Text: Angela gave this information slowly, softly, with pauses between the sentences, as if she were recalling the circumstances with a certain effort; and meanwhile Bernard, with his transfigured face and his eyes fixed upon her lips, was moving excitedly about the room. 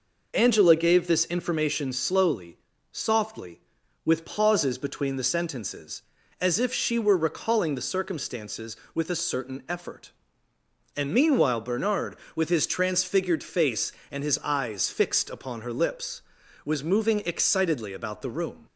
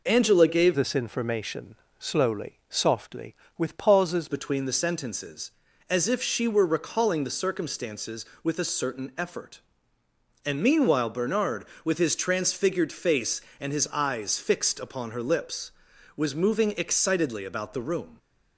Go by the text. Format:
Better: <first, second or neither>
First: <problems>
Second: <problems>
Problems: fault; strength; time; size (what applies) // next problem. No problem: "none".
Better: first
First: none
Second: changes voice from "this" to "pauses"; from 0.7 to 4.2 s; 3.5 s long // pauses between "information" and "slowly"; slight; at 1.7 s; 0.24 s long